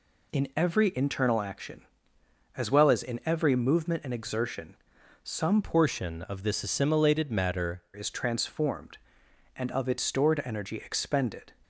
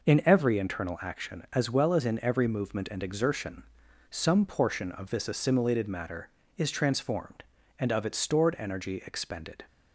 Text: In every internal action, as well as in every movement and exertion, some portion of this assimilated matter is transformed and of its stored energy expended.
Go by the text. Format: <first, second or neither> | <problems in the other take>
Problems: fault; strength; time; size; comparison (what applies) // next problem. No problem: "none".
second | changes voice from "portion" to "matter"; from 5.6 to 7.8 s; 2.2 s long